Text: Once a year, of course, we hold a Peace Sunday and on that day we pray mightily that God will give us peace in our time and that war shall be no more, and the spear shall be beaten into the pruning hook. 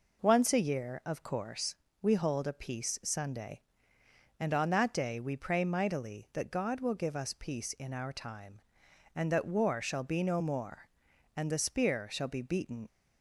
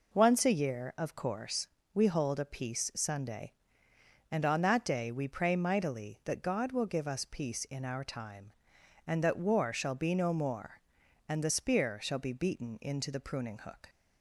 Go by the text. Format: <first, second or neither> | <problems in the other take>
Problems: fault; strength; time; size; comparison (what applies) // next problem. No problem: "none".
second | stops before "into the pruning hook"; at 12.8 s